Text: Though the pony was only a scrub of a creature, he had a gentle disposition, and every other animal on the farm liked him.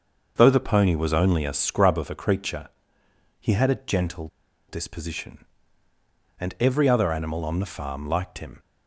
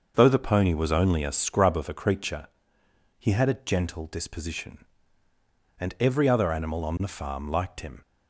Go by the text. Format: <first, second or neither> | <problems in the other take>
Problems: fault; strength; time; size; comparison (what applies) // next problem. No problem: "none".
second | starts louder than the rest; until 1.3 s; 6.5 dB; also in the second // pauses between "gentle" and "disposition"; at 4.2 s; 0.41 s long